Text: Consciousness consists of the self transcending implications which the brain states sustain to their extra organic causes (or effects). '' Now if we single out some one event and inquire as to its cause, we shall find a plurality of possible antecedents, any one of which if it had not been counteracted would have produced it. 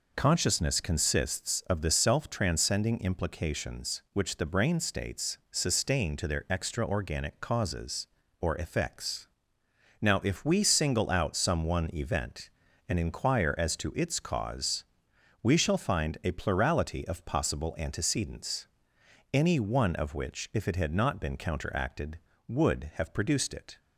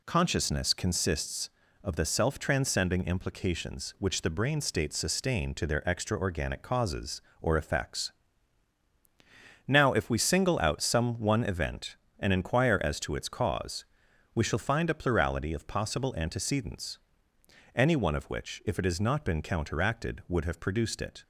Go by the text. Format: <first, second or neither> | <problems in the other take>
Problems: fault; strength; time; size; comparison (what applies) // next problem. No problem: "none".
first | says "has" for "had"; at 18.8 s